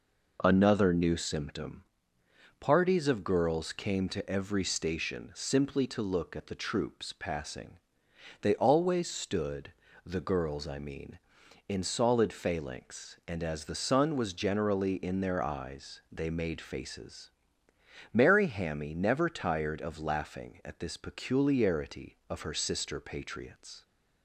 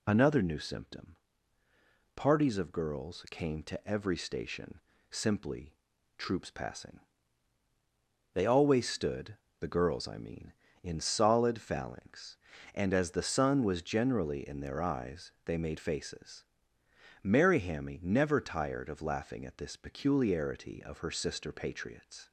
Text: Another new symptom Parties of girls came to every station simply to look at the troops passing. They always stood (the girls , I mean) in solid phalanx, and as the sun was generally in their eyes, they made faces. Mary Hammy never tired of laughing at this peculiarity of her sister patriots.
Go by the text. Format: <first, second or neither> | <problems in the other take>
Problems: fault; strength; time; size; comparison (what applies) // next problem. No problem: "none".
first | pauses between "symptom" and "Parties"; at 1.1 s; 1.0 s long; noticeable in the first // pauses between "station" and "simply"; slight; at 4.8 s; 0.30 s long // skips "to look at the"; at 5.9 s